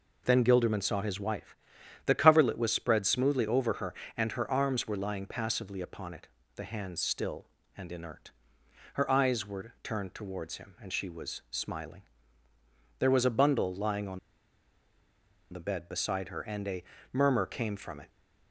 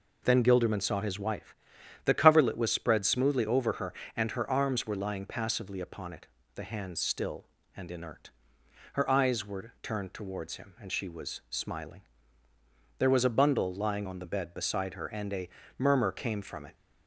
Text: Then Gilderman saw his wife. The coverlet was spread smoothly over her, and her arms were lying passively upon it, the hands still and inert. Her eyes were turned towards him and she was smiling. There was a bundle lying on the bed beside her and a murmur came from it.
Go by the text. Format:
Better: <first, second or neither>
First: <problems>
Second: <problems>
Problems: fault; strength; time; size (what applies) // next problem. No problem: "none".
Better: second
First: pauses between "on" and "the"; strong; at 14.1 s; 1.3 s long // pauses between "a" and "murmur"; slight; at 16.8 s; 0.30 s long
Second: pauses between "a" and "murmur"; slight; at 15.4 s; 0.30 s long